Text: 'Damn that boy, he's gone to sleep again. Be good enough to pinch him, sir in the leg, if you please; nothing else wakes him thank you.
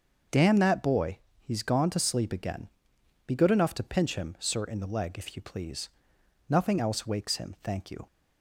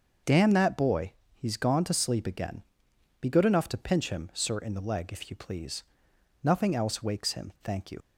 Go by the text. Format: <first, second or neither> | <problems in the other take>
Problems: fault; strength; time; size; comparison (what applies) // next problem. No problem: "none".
first | starts louder than the rest; until 1.4 s; 6.5 dB; also in the first // leaves "you" unfinished; at 8.0 s; 65 ms